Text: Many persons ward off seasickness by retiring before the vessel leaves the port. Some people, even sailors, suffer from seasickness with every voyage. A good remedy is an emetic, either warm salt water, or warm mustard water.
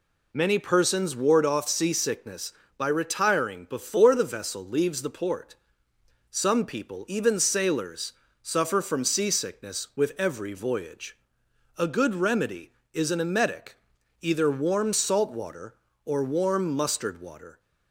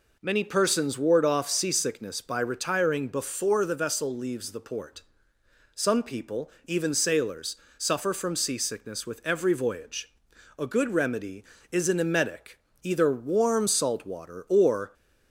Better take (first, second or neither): first